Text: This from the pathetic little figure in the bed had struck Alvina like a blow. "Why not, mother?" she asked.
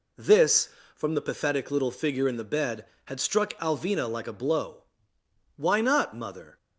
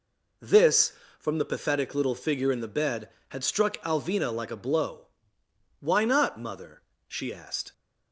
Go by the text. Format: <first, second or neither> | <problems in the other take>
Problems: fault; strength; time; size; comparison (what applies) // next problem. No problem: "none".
second | stops before "she asked"; at 6.5 s